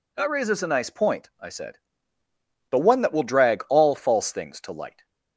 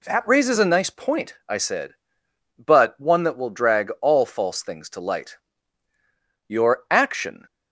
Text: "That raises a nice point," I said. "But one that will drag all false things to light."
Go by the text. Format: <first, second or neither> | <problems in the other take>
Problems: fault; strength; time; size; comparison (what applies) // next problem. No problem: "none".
first | goes on to say "Your action"; noticeable; from 6.4 s on; 0.98 s long